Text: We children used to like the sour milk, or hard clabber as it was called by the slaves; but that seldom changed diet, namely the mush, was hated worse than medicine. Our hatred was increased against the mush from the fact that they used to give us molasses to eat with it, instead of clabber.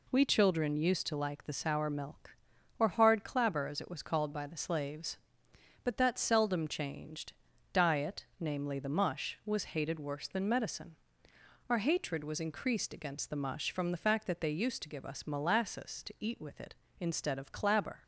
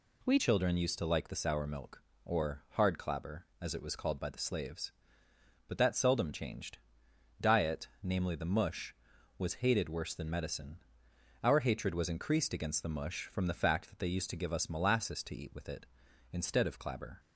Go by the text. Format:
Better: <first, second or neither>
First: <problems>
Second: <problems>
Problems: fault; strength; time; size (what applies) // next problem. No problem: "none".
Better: first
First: pauses between "changed" and "diet"; at 7.3 s; 0.40 s long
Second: changes voice at "children"; from 0.3 s on; 16.8 s long // pauses between "changed" and "diet"; noticeable; at 6.7 s; 0.60 s long